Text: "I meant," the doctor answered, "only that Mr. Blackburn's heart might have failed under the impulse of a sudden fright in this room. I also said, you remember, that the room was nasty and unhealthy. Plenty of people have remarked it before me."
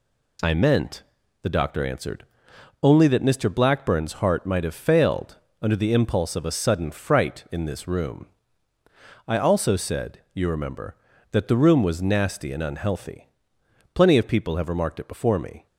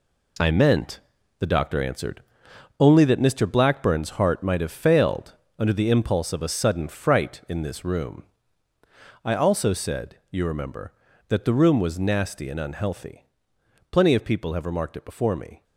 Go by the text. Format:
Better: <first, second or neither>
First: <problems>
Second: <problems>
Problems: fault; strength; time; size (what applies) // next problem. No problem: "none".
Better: first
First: pauses between "failed" and "under"; slight; at 5.3 s; 0.24 s long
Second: gets quieter; strong; throughout; 9 dB // pauses between "failed" and "under"; slight; at 5.3 s; 0.24 s long